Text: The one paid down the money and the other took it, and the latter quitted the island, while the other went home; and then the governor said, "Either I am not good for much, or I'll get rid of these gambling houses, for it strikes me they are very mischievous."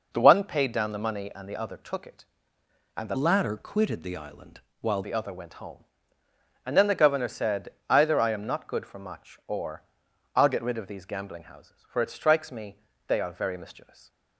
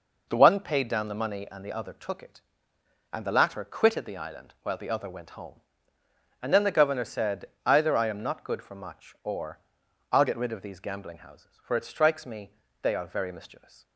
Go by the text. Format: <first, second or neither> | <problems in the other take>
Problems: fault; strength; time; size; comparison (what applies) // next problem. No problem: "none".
second | changes voice from "latter" to "while"; from 3.1 to 5.0 s; 1.9 s long // pauses between "or" and "I'll"; noticeable; at 9.8 s; 0.52 s long; noticeable in the second // pauses between "me" and "they"; slight; at 12.7 s; 0.26 s long; slight in the second